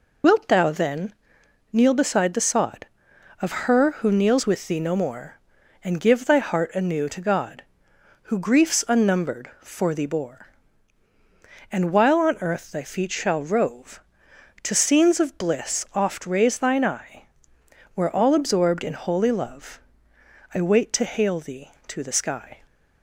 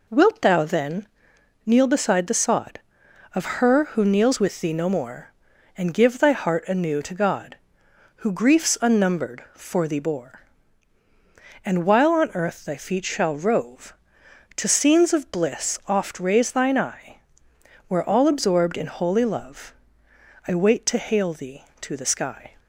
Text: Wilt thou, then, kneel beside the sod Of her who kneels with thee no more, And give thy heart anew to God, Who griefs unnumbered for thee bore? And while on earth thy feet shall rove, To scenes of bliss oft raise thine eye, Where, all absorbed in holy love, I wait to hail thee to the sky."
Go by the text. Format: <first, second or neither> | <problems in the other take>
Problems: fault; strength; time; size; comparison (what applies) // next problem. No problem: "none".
second | loses the start of "Wilt"; at 0.2 s; 80 ms